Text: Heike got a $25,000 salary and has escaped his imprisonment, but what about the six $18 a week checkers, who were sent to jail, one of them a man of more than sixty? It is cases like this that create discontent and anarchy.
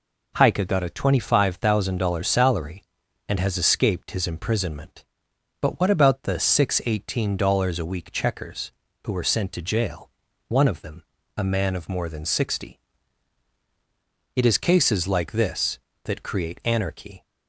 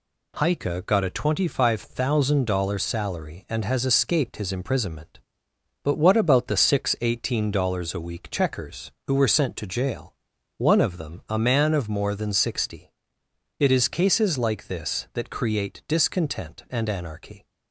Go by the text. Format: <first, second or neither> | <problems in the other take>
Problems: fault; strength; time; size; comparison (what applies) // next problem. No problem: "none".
second | pauses between "them" and "a"; slight; at 11.0 s; 0.34 s long // skips "discontent and"; at 16.6 s